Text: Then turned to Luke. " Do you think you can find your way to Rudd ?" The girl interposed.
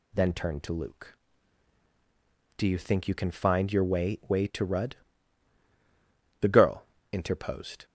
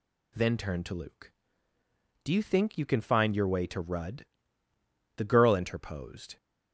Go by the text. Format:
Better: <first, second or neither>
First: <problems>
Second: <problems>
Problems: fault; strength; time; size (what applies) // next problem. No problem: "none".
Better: second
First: says "way" twice; at 4.2 s // pauses between "girl" and "interposed"; slight; at 6.8 s; 0.26 s long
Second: none